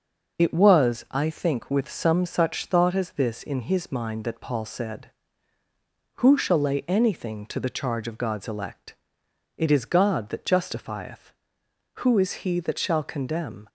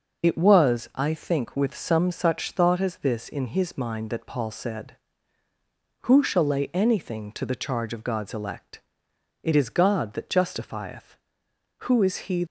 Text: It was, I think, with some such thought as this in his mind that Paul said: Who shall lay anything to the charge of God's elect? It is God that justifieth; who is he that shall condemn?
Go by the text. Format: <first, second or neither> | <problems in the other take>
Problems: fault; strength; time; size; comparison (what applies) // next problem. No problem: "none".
first | stops before "that shall condemn"; at 12.4 s